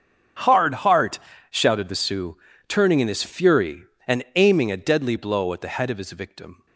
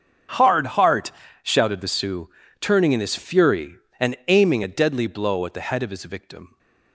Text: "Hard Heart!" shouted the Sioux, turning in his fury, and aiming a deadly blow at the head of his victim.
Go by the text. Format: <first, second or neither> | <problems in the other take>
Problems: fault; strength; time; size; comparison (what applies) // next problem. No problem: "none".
neither | starts louder than the rest; strong; the same in both